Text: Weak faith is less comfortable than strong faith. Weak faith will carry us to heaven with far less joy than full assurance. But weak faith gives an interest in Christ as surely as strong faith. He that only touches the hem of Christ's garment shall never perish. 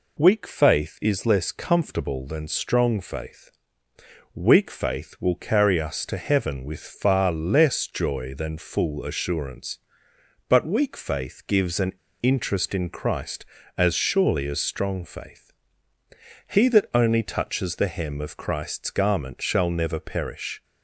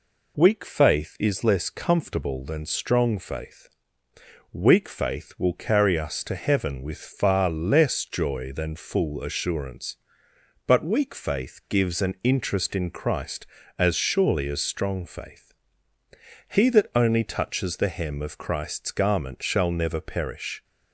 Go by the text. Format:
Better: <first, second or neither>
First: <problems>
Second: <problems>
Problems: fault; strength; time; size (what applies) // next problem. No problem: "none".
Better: second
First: pauses between "an" and "interest"; slight; at 11.9 s; 0.30 s long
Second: none